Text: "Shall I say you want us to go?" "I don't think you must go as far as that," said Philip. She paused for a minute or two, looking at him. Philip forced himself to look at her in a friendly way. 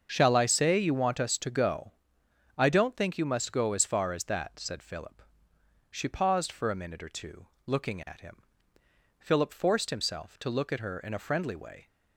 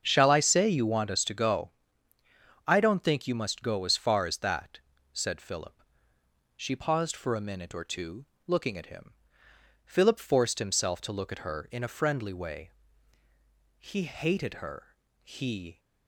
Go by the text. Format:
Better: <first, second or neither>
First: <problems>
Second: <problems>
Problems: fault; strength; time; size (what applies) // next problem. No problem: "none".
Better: first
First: starts louder than the rest; until 1.1 s; 7 dB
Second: starts louder than the rest; until 1.0 s; 7 dB // goes on to say "He hated her he"; strong; from 13.8 s on; 1.9 s long